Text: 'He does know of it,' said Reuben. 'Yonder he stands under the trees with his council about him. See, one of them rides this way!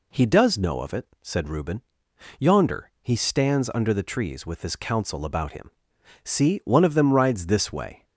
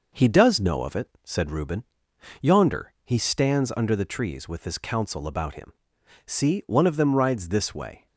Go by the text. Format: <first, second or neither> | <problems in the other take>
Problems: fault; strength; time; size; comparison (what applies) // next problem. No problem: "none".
first | gets quieter; slight; throughout; 3 dB